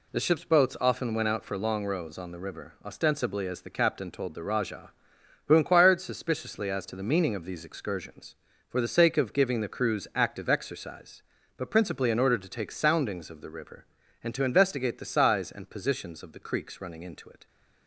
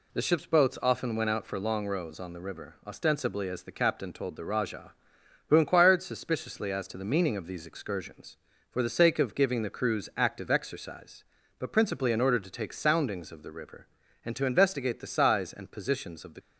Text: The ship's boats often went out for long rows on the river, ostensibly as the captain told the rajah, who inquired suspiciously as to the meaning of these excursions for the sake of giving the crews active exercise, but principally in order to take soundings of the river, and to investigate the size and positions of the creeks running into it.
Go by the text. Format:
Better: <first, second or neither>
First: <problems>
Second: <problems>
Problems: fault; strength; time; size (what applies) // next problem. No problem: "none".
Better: first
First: none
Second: stops before "creeks running into it"; at 16.3 s